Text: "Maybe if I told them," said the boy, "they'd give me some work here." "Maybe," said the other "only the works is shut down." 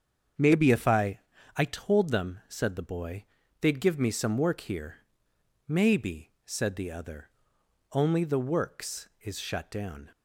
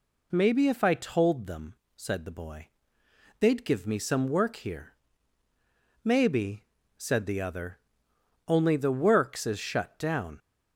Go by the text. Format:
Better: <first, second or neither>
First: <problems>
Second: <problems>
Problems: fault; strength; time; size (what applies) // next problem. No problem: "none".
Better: second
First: starts louder than the rest; strong; until 1.7 s; 7.5 dB // says "I" twice; at 1.5 s // pauses between "other" and "only"; noticeable; at 7.2 s; 0.64 s long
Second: pauses between "other" and "only"; noticeable; at 7.8 s; 0.66 s long